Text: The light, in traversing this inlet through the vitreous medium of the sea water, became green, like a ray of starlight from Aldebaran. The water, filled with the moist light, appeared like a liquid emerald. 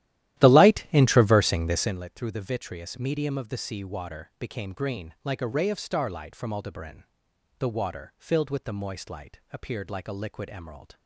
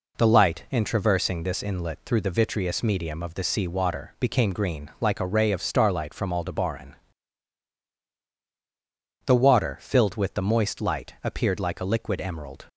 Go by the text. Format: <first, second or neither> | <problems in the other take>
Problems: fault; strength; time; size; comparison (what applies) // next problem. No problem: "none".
second | starts louder than the rest; strong; until 2.0 s; 13.5 dB